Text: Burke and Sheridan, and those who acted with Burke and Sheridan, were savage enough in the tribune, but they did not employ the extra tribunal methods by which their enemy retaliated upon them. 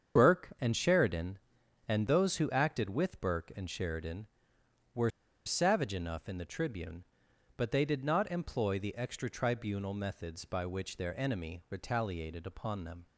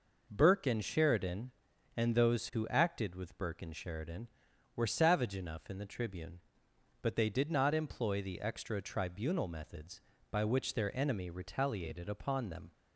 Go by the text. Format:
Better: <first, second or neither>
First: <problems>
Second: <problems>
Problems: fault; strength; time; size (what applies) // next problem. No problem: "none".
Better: second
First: starts louder than the rest; strong; until 1.2 s; 7.5 dB // pauses between "were" and "savage"; slight; at 5.1 s; 0.35 s long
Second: none